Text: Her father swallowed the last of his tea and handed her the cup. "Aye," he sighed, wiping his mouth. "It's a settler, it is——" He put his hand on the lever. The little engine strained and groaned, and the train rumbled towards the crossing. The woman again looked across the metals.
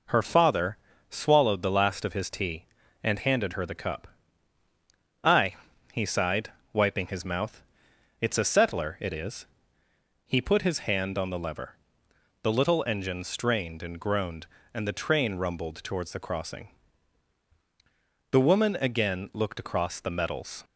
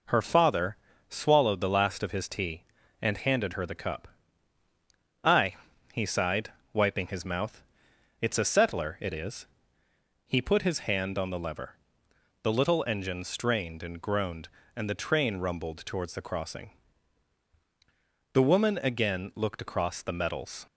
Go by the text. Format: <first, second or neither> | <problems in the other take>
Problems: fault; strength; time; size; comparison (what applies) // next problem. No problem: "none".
neither | pauses between "father" and "swallowed"; slight; the same in both